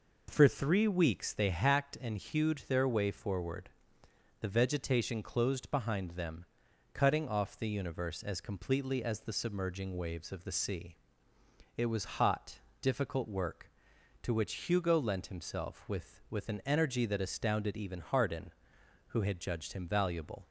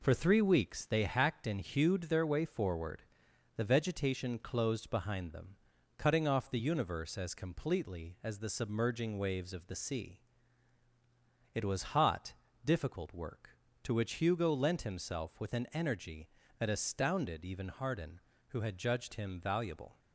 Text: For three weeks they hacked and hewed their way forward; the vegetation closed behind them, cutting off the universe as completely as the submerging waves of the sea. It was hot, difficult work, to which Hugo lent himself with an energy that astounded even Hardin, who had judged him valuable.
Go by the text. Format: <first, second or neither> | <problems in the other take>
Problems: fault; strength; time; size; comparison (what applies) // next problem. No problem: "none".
second | says "with" twice; at 16.2 s